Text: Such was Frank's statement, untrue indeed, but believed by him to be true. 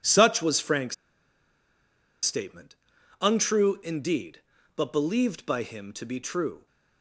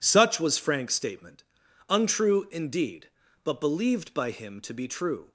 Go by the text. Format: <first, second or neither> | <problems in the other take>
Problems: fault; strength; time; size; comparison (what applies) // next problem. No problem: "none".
second | pauses between "Frank's" and "statement"; strong; at 0.9 s; 1.3 s long